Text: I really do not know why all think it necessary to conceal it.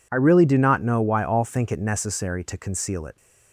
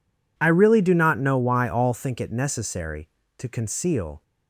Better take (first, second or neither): first